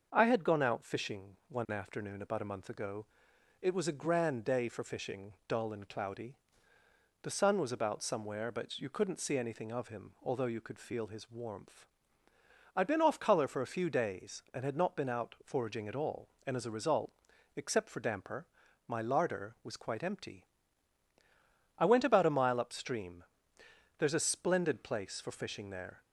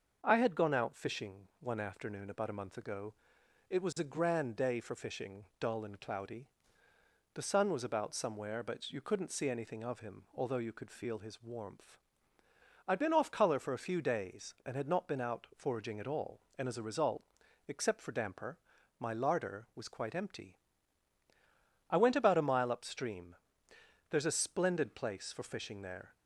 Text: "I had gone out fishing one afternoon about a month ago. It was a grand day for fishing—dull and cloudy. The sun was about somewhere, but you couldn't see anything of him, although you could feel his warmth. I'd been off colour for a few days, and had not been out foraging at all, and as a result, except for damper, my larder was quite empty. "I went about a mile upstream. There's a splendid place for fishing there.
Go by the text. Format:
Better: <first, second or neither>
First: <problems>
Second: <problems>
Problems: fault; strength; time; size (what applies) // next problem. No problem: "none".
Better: neither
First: starts louder than the rest; until 1.1 s; 6.5 dB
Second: starts louder than the rest; until 1.2 s; 6.5 dB